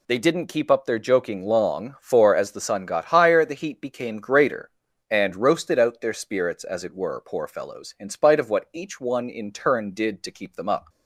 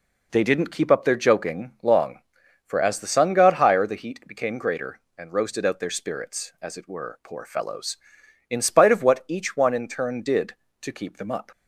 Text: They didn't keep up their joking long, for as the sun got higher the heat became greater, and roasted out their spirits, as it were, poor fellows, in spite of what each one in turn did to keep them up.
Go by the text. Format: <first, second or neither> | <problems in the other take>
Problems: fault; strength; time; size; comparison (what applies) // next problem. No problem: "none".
neither | none